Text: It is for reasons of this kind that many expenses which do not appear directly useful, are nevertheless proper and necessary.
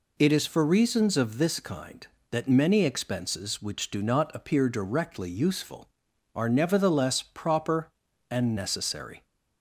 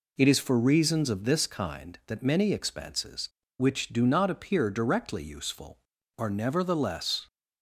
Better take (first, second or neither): first